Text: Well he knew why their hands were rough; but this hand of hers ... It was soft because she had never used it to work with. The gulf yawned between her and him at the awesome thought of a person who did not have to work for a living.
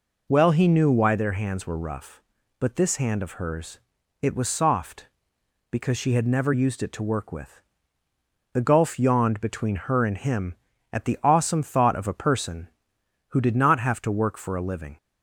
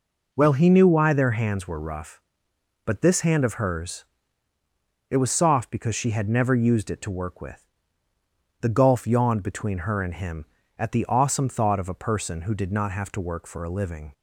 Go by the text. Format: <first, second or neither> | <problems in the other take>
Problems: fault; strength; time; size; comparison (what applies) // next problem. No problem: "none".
neither | none